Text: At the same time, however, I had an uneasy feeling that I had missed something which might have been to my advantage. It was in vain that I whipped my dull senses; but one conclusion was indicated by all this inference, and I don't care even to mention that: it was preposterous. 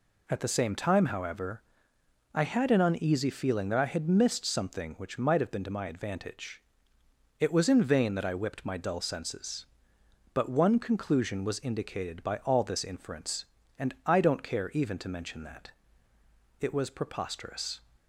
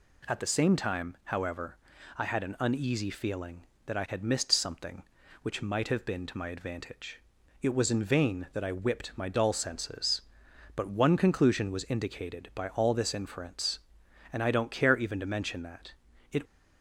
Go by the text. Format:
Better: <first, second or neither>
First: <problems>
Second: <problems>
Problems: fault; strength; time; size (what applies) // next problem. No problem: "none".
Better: first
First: none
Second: stops before "was preposterous"; at 16.4 s